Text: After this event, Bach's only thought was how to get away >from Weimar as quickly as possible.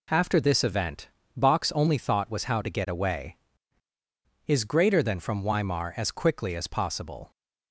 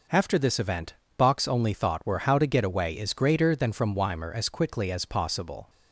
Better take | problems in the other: first | says "were" for "was"; at 2.0 s

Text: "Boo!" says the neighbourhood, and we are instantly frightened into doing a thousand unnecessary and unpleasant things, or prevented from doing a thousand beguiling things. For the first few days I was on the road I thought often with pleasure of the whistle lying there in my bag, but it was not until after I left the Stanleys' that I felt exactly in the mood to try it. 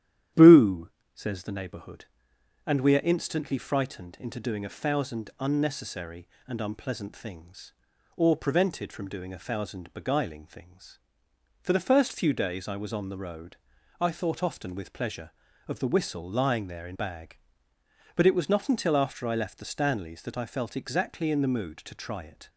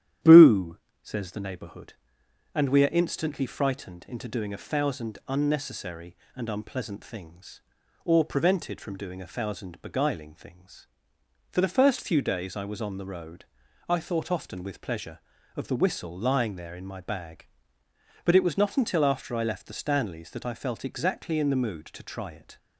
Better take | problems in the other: second | starts louder than the rest; strong; until 1.5 s; 11 dB; strong in the second // pauses between "road" and "I"; at 13.5 s; 0.44 s long; also in the second // skips "my"; at 16.9 s

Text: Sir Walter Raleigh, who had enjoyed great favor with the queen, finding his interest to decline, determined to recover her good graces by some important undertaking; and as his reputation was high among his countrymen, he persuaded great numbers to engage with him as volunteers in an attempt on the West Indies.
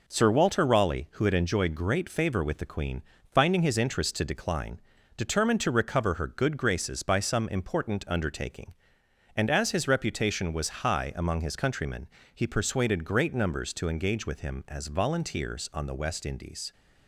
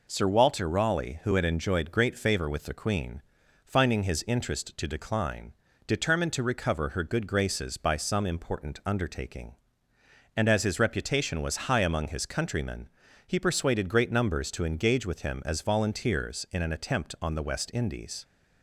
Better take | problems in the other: second | skips "in an attempt"; at 15.7 s

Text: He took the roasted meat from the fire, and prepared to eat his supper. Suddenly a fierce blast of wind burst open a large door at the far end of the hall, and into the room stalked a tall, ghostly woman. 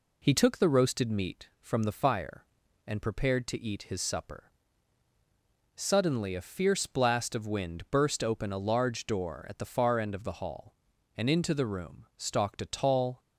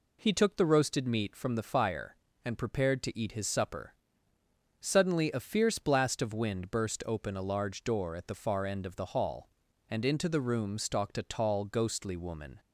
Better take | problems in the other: second | stops before "ghostly woman"; at 13.2 s

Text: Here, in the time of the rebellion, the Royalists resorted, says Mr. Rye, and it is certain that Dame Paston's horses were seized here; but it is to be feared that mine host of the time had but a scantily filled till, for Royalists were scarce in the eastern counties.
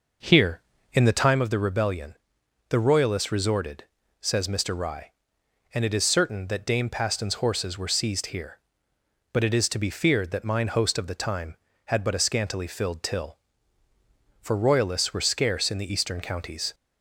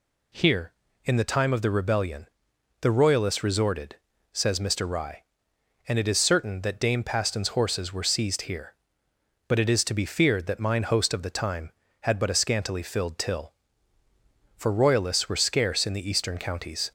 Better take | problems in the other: second | starts louder than the rest; noticeable; until 1.4 s; 5.5 dB

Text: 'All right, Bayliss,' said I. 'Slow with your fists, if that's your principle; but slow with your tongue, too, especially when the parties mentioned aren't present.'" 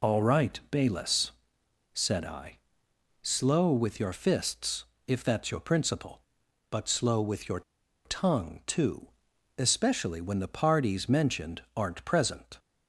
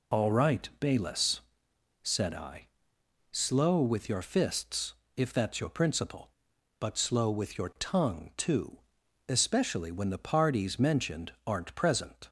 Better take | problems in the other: second | pauses between "your" and "tongue"; at 7.6 s; 0.43 s long

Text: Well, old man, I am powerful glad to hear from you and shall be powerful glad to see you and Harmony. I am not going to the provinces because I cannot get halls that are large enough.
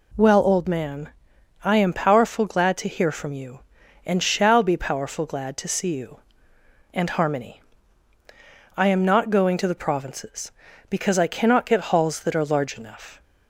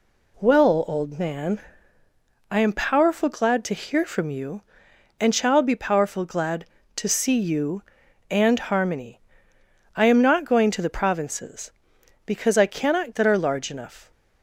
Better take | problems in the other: first | skips "get halls"; at 13.1 s

